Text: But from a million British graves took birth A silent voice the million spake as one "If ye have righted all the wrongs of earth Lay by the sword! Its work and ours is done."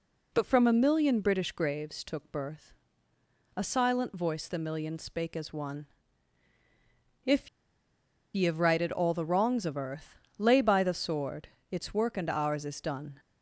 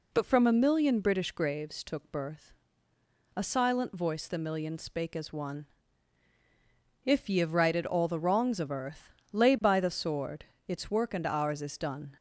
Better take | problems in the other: second | pauses between "birth" and "A"; noticeable; at 2.7 s; 0.82 s long; noticeable in the second // pauses between "one" and "If"; strong; at 5.8 s; 1.3 s long; strong in the second // pauses between "If" and "ye"; noticeable; at 7.4 s; 0.86 s long // pauses between "earth" and "Lay"; slight; at 10.1 s; 0.22 s long; slight in the second

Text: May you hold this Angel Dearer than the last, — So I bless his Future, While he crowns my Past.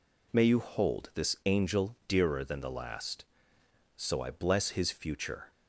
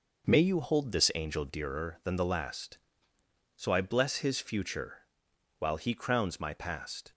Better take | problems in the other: second | stops before "While he crowns my Past"; at 5.5 s

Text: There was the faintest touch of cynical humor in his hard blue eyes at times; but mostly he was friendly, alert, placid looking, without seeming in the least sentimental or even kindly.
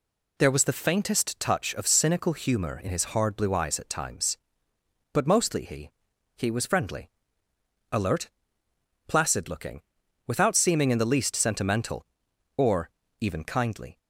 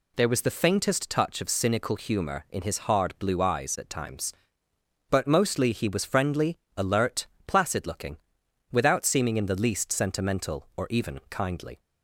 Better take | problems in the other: second | says "he" twice; at 6.3 s // pauses between "or" and "even"; slight; at 12.8 s; 0.30 s long

